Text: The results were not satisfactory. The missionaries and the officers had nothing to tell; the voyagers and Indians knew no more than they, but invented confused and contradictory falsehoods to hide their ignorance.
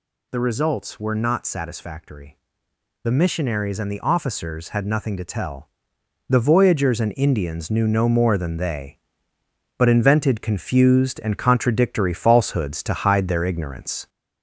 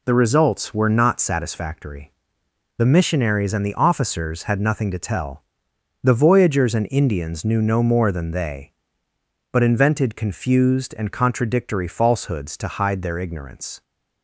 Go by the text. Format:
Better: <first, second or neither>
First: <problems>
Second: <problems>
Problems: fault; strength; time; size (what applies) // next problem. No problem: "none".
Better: second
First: gets louder; throughout; 3.5 dB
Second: none